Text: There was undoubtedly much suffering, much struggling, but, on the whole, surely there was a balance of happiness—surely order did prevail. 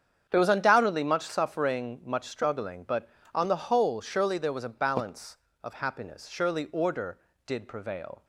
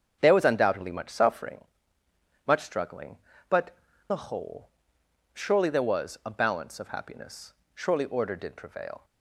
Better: first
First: starts louder than the rest; strong; until 1.3 s; 8 dB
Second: starts louder than the rest; strong; until 1.2 s; 7 dB // skips "on"; at 3.9 s

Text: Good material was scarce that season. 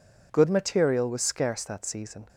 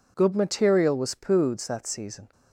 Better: first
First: none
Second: says "poods" for "scarce"; at 1.1 s

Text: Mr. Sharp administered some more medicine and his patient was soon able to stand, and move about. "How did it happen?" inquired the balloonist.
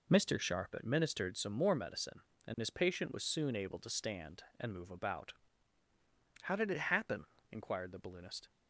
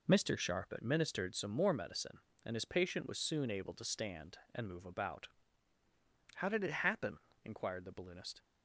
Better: neither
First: none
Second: none

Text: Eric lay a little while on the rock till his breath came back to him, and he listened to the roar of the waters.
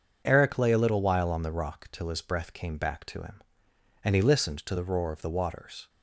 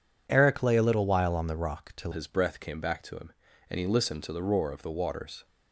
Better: first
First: none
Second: changes voice at "his"; from 2.1 s on; 3.3 s long

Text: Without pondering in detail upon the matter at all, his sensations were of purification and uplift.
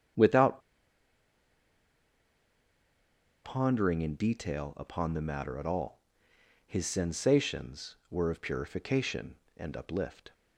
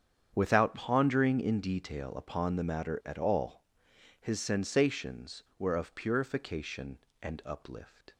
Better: second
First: starts louder than the rest; strong; until 4.0 s; 7.5 dB // pauses between "Without" and "pondering"; strong; at 0.6 s; 2.8 s long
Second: starts louder than the rest; strong; until 1.3 s; 8 dB

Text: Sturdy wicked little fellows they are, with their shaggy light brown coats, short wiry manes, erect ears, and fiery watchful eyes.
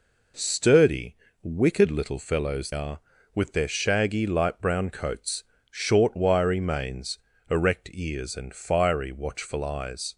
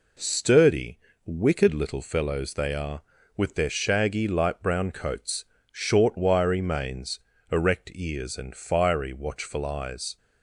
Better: second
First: pauses between "Sturdy" and "wicked"; slight; at 1.1 s; 0.28 s long // skips "they"; at 2.7 s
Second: pauses between "Sturdy" and "wicked"; slight; at 0.9 s; 0.28 s long

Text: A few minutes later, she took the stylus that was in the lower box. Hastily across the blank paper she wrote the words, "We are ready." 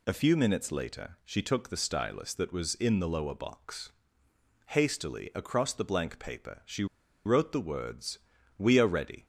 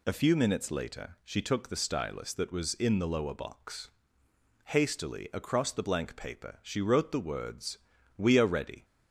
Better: second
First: pauses between "she" and "wrote"; at 6.8 s; 0.40 s long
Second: none

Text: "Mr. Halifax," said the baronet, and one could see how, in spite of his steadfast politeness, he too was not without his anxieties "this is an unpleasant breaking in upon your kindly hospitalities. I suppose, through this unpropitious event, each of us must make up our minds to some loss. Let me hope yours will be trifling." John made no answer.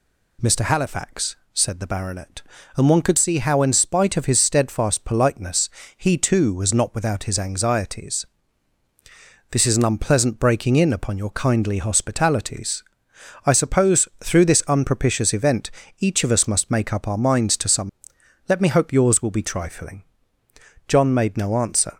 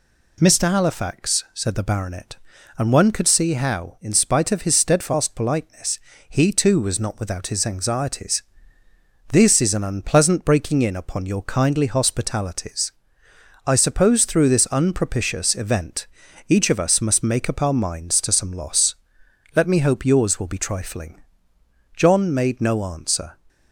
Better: second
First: pauses between "anxieties" and "this"; strong; at 8.2 s; 1.2 s long // skips "loss"; at 18.1 s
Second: pauses between "anxieties" and "this"; noticeable; at 8.4 s; 0.90 s long

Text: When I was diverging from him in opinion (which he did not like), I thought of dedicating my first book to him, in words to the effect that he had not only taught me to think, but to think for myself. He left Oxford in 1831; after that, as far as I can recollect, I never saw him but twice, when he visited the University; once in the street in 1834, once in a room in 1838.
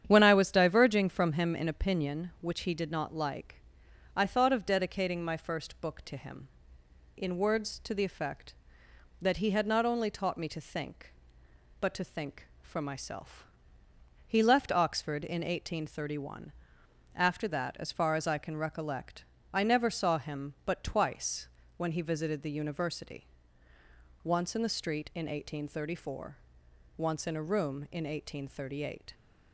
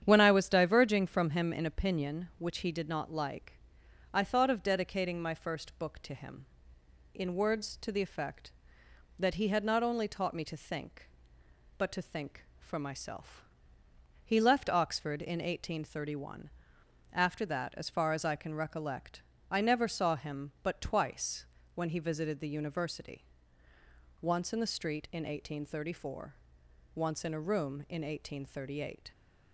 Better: neither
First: starts louder than the rest; strong; until 1.0 s; 9 dB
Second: starts louder than the rest; strong; until 1.0 s; 9 dB

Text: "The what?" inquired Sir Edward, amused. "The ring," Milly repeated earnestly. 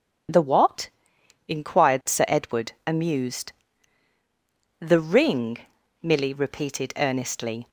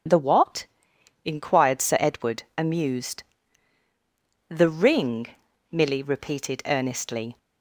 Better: neither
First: none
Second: none

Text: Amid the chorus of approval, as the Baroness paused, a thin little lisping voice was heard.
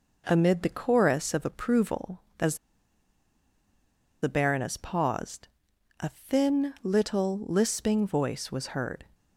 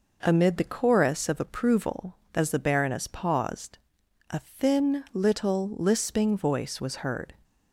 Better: second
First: pauses between "as" and "the"; strong; at 2.5 s; 1.6 s long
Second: none

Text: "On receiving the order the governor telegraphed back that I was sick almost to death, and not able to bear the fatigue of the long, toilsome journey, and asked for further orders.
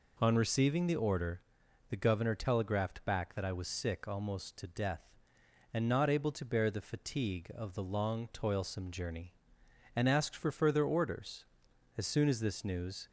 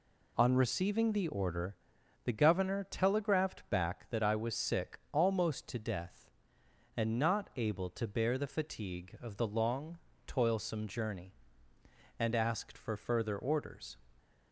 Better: second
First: pauses between "order" and "the"; noticeable; at 1.4 s; 0.48 s long // goes on to say "As soon as this news"; noticeable; from 11.9 s on; 1.1 s long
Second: pauses between "order" and "the"; noticeable; at 1.7 s; 0.50 s long

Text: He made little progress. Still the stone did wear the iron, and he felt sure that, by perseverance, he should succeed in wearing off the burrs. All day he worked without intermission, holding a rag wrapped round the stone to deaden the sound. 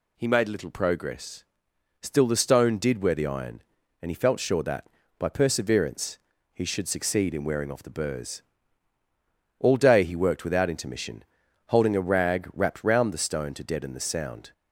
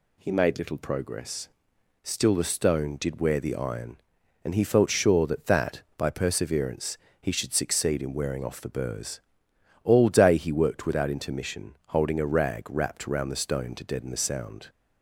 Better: first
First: none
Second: says "that" twice; at 5.4 s

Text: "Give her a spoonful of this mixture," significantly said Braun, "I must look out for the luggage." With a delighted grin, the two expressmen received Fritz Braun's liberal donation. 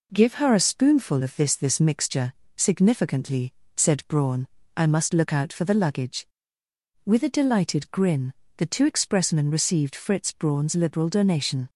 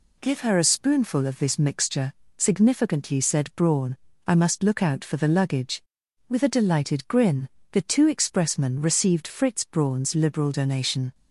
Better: second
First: says "this" twice; at 1.5 s // pauses between "significantly" and "said"; slight; at 3.5 s; 0.22 s long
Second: none

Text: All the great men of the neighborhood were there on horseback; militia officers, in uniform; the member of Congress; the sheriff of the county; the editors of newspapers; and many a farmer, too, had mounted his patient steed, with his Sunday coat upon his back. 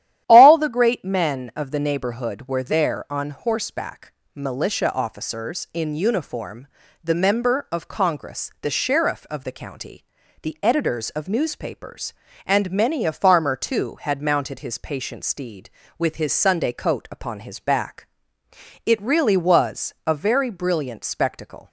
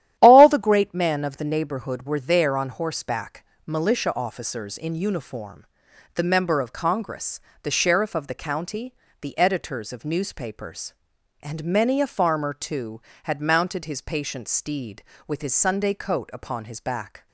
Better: second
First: starts louder than the rest; strong; until 1.2 s; 11.5 dB // goes on to say "It really was a very brilliant spectacle"; strong; from 18.8 s on; 2.8 s long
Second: starts louder than the rest; strong; until 1.2 s; 12 dB

